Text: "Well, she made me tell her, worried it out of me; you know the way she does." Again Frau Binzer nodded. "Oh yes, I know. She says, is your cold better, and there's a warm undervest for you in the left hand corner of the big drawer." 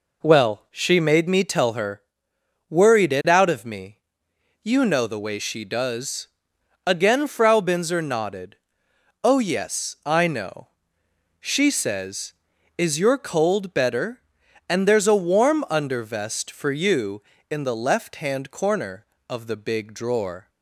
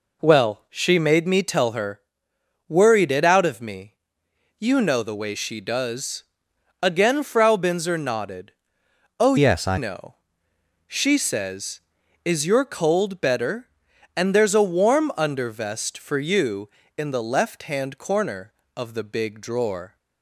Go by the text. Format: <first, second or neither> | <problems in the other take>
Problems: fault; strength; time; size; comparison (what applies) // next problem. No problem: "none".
first | changes voice from "yes" to "I"; from 9.3 to 9.7 s; 0.4 s long